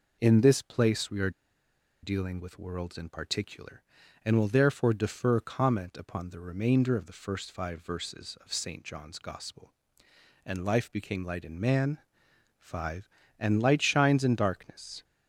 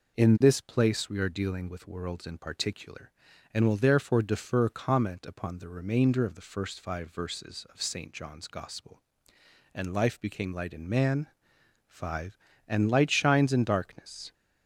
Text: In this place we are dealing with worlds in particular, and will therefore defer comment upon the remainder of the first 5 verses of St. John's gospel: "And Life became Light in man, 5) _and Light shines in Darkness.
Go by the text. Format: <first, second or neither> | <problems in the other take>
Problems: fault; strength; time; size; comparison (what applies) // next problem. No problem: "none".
second | pauses between "are" and "dealing"; noticeable; at 1.2 s; 0.73 s long